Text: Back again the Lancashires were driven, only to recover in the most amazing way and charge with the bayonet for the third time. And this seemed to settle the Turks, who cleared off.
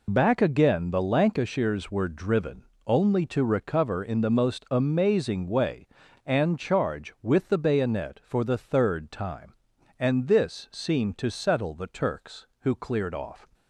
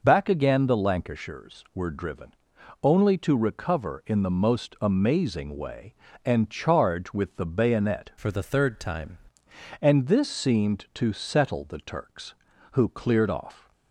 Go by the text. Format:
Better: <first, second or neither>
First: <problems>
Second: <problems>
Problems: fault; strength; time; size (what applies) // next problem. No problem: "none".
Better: first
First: none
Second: changes voice from "for" to "time"; from 8.1 to 9.1 s; 1.0 s long